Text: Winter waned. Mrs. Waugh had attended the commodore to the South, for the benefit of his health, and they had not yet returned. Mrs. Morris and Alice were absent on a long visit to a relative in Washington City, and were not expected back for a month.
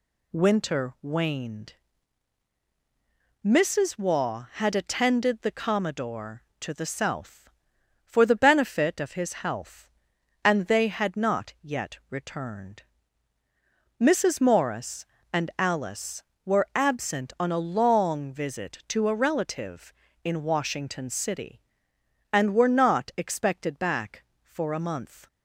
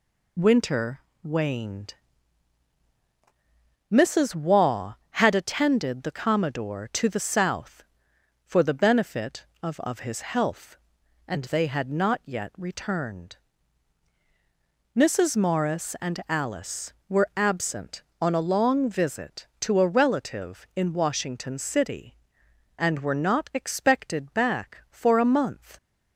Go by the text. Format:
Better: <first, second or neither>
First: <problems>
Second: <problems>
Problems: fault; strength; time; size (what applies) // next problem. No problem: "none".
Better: first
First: none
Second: pauses between "Winter" and "waned"; slight; at 0.9 s; 0.24 s long // says "of" twice; at 9.8 s